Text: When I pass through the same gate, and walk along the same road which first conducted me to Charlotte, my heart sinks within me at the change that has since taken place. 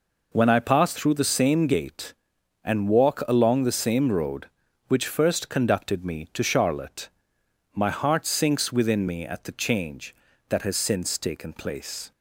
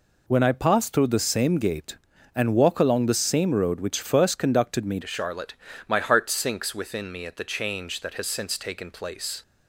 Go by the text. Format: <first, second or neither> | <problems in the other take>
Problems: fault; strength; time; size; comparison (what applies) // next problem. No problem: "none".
first | changes voice at "to"; from 5.0 s on; 4.4 s long